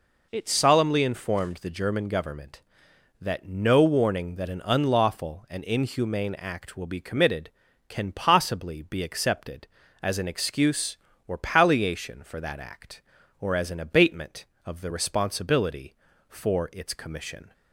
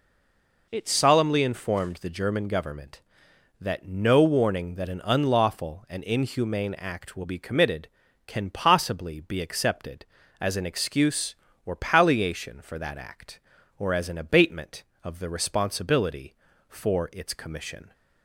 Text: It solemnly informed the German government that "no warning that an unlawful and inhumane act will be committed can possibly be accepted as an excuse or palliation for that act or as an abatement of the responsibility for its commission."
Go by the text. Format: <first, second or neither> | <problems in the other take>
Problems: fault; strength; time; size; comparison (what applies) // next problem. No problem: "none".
first | stays silent before the first word; slight; until 0.6 s; 0.6 s long